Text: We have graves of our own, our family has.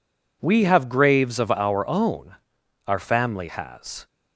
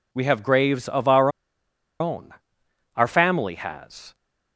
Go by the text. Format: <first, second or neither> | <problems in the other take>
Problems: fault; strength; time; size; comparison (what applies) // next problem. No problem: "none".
first | pauses between "our" and "own"; noticeable; at 1.2 s; 0.70 s long